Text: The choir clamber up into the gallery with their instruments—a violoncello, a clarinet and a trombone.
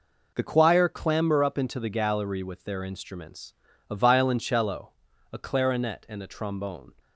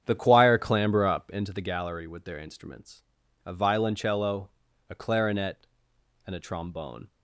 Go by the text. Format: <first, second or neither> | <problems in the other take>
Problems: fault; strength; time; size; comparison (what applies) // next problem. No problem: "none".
first | starts louder than the rest; strong; until 1.6 s; 8.5 dB